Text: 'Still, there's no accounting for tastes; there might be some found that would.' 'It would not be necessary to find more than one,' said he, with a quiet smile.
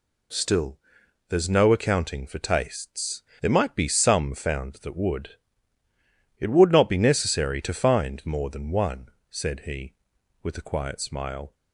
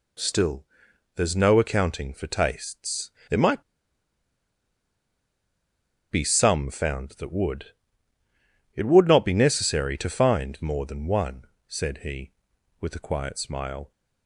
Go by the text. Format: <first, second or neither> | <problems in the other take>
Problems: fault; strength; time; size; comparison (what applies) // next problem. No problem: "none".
first | pauses between "might" and "be"; strong; at 3.6 s; 2.4 s long